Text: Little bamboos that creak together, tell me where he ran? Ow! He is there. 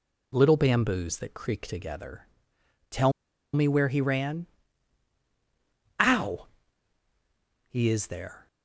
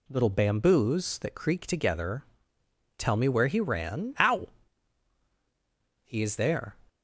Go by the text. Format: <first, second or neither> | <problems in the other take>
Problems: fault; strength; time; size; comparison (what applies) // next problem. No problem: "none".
second | pauses between "tell" and "me"; at 3.1 s; 0.43 s long